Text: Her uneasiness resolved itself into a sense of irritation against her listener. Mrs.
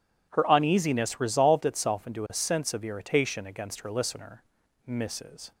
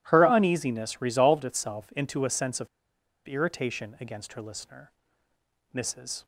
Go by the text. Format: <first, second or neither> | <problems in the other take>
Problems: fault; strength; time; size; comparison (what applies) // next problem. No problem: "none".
first | pauses between "of" and "irritation"; noticeable; at 2.6 s; 0.58 s long